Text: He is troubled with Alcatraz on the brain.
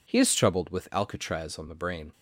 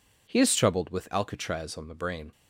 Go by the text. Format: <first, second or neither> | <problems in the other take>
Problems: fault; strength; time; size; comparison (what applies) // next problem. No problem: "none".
neither | none